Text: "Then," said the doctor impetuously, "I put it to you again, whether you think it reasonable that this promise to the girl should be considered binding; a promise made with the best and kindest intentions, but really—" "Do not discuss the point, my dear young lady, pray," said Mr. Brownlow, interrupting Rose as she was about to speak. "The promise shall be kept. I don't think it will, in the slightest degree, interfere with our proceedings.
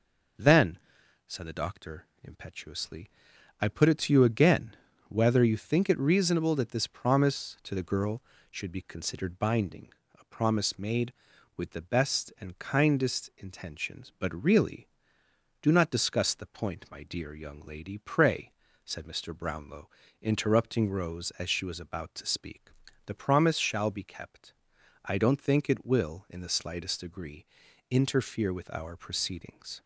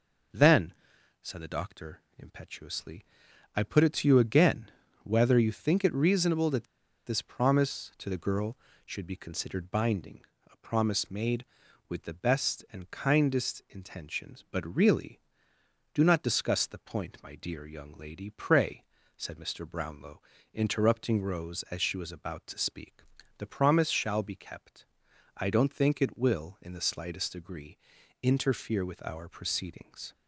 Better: first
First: pauses between "doctor" and "impetuously"; slight; at 2.0 s; 0.18 s long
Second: pauses between "doctor" and "impetuously"; slight; at 2.0 s; 0.18 s long // pauses between "that" and "this"; at 6.6 s; 0.41 s long

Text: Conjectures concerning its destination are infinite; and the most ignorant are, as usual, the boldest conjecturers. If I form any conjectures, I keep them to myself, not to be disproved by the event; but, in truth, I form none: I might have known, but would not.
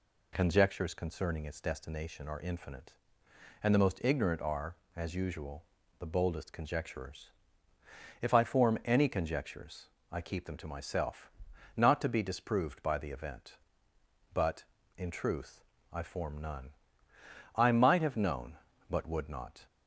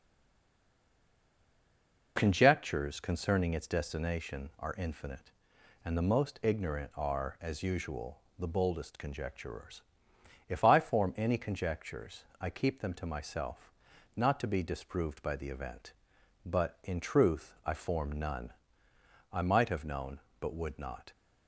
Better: first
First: none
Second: stays silent before the first word; until 2.1 s; 2.1 s long

